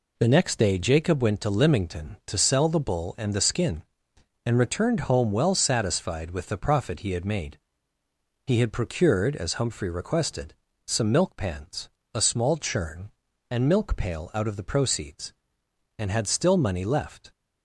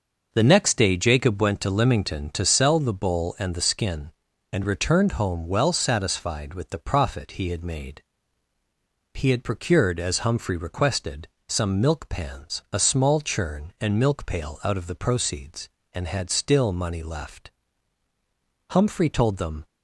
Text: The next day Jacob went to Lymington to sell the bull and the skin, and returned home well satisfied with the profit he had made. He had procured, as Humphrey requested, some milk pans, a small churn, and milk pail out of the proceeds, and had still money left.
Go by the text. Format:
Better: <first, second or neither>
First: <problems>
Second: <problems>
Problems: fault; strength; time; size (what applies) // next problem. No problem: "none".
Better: first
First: none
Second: goes on to say "Humphrey told them"; noticeable; from 18.6 s on; 0.96 s long